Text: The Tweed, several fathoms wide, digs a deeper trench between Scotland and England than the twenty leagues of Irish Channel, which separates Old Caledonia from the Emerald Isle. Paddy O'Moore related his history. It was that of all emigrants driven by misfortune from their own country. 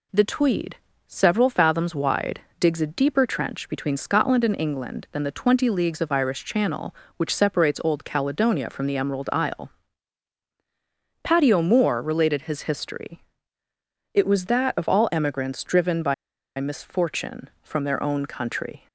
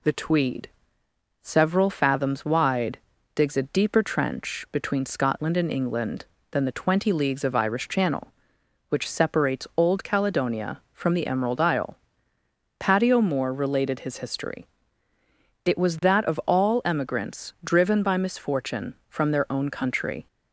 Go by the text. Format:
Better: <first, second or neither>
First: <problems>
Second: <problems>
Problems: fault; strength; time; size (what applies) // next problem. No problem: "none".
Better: second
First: pauses between "by" and "misfortune"; at 16.1 s; 0.44 s long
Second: none